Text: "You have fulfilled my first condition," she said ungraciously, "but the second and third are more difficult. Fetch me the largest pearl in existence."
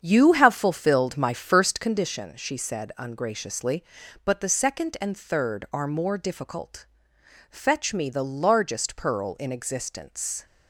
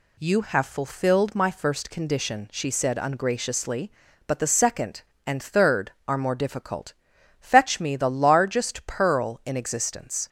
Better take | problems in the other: second | starts louder than the rest; strong; until 1.9 s; 7.5 dB

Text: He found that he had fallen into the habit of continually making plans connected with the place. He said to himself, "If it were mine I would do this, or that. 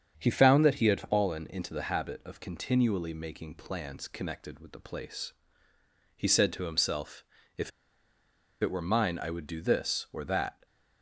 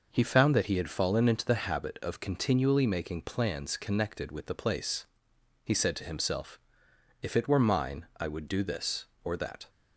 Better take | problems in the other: second | starts louder than the rest; strong; until 1.1 s; 7.5 dB // pauses between "If" and "it"; noticeable; at 7.7 s; 0.90 s long

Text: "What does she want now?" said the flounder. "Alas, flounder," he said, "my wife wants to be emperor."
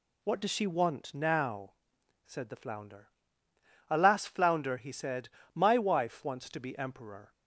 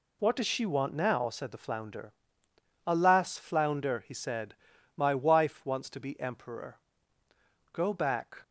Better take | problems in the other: first | goes on to say "Go back"; noticeable; from 7.7 s on; 0.70 s long

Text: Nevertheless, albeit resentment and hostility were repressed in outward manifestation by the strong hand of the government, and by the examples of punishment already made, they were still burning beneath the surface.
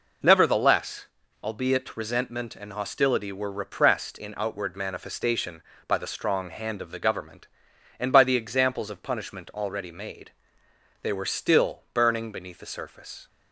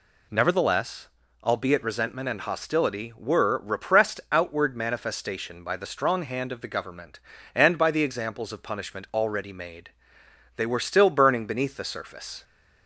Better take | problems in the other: first | skips "in"; at 4.2 s

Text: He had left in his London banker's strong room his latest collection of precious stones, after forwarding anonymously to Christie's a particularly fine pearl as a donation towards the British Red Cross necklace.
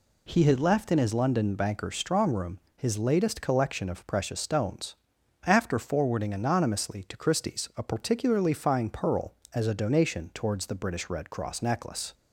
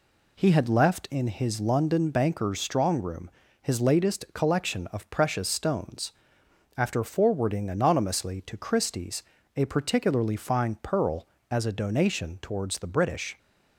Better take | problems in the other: first | pauses between "room" and "his"; slight; at 3.2 s; 0.32 s long; slight in the first // pauses between "Christie's" and "a"; slight; at 9.2 s; 0.32 s long // stops before "Red Cross necklace"; at 13.3 s

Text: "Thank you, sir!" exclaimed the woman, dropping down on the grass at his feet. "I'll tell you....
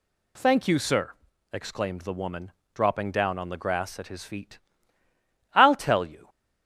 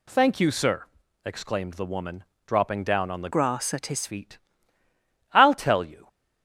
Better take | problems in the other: first | changes voice from "grass" to "his"; from 3.3 to 4.0 s; 0.7 s long

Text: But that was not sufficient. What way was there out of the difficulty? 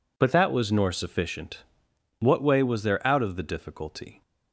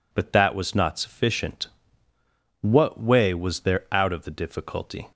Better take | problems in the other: second | says "nor" for "not"; at 0.7 s

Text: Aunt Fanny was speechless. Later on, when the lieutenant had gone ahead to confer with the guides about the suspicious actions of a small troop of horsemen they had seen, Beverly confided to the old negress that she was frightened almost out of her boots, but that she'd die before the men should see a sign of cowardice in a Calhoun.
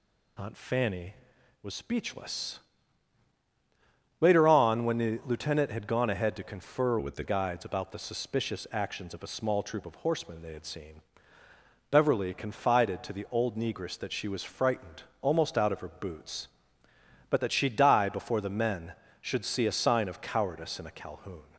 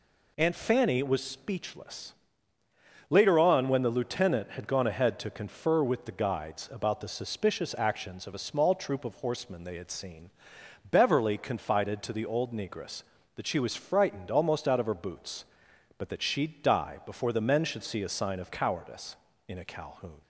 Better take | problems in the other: second | changes voice from "with" to "the"; from 6.9 to 7.2 s; 0.3 s long // pauses between "frightened" and "almost"; slight; at 15.0 s; 0.18 s long

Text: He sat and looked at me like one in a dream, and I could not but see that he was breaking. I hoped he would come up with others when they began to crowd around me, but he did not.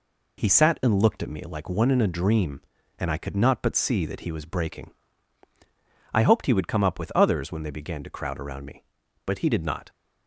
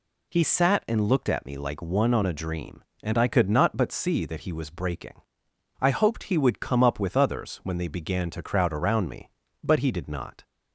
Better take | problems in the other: first | says "on" for "in"; at 2.1 s

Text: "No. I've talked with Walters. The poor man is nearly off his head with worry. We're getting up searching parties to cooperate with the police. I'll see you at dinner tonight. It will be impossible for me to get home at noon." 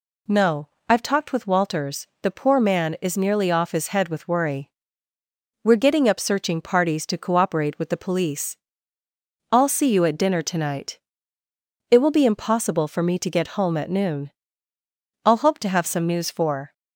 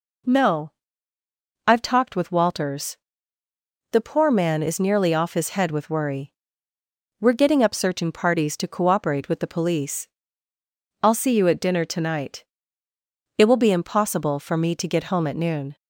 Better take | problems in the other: second | goes on to say "I'll hope to have some news for"; from 15.2 s on; 1.4 s long

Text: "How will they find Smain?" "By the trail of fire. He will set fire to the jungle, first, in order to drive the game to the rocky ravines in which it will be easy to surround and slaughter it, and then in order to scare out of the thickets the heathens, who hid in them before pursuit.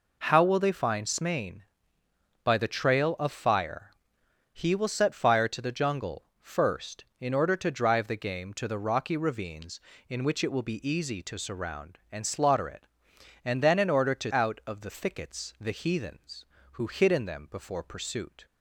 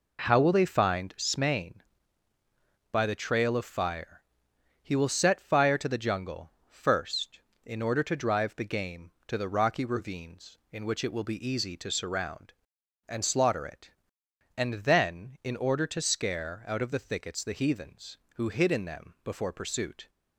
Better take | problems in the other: second | skips "scare"; at 14.3 s

